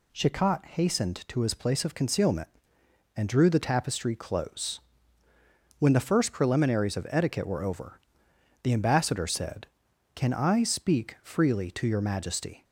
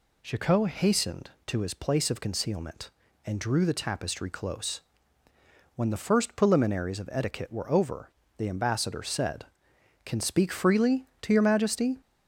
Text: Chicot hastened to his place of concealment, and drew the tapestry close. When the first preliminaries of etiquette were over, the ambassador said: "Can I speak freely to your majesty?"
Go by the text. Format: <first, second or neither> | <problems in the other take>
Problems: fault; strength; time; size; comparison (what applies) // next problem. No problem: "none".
first | skips "I"; at 10.1 s